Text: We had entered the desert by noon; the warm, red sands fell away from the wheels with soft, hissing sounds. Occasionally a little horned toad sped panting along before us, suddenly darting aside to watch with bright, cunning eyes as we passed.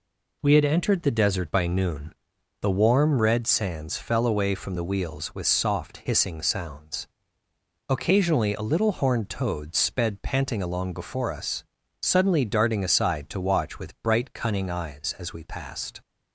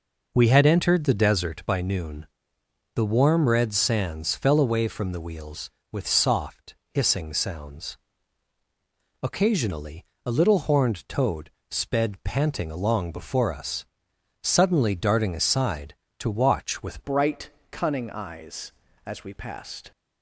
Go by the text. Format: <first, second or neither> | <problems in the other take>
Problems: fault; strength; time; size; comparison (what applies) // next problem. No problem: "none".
first | pauses between "Occasionally" and "a"; slight; at 10.0 s; 0.18 s long // pauses between "toad" and "sped"; slight; at 11.5 s; 0.18 s long // changes voice at "bright"; from 17.0 s on; 2.9 s long